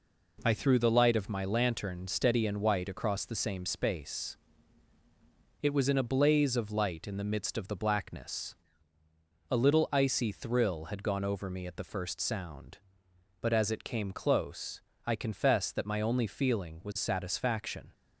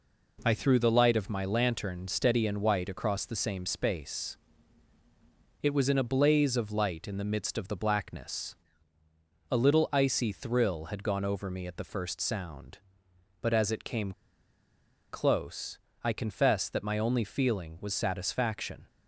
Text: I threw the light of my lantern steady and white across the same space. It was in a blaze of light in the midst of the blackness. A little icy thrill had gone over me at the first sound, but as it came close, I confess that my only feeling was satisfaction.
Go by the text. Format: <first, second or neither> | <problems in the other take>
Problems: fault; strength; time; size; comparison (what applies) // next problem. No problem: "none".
first | pauses between "came" and "close"; at 14.1 s; 1.0 s long